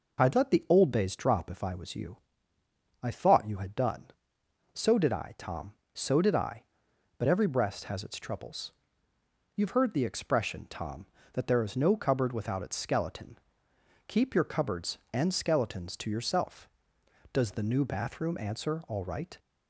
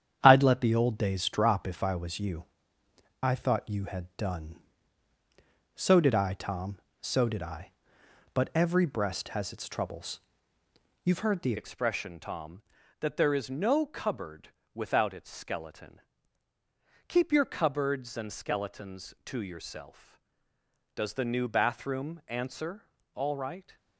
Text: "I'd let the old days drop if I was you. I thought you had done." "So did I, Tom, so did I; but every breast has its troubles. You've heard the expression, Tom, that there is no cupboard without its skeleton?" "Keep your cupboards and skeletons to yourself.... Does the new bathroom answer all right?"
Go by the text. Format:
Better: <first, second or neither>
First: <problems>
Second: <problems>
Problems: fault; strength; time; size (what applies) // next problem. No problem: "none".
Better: first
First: none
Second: starts louder than the rest; strong; until 1.2 s; 9 dB // changes voice at "expression"; from 11.5 s on; 12.2 s long // pauses between "cupboard" and "without"; slight; at 14.5 s; 0.22 s long // pauses between "answer" and "all"; slight; at 22.8 s; 0.30 s long